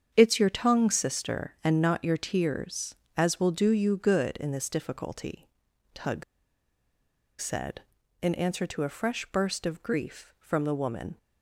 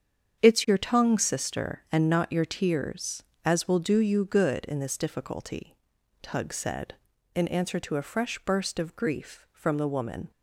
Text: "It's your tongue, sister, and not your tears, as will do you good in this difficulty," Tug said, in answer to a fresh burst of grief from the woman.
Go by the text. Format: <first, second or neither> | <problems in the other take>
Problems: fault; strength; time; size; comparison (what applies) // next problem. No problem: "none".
second | starts louder than the rest; strong; until 1.1 s; 8 dB; strong in the second // pauses between "Tug" and "said"; at 6.2 s; 1.1 s long